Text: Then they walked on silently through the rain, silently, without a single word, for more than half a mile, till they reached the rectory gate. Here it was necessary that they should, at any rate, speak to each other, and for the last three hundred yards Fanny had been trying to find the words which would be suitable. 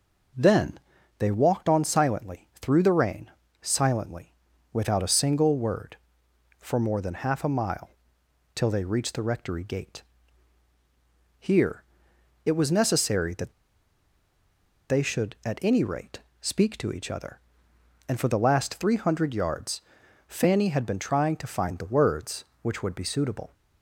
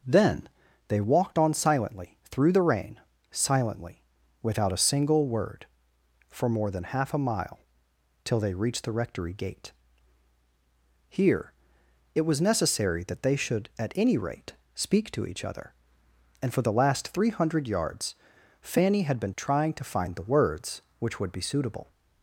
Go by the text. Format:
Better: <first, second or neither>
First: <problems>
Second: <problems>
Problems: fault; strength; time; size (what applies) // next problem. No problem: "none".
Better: second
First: pauses between "Then" and "they"; at 0.7 s; 0.40 s long // pauses between "Here" and "it"; noticeable; at 11.8 s; 0.62 s long // pauses between "that" and "they"; strong; at 13.5 s; 1.3 s long // pauses between "yards" and "Fanny"; noticeable; at 19.8 s; 0.46 s long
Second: pauses between "Then" and "they"; at 0.4 s; 0.40 s long // pauses between "Here" and "it"; noticeable; at 11.5 s; 0.62 s long // pauses between "yards" and "Fanny"; noticeable; at 18.1 s; 0.46 s long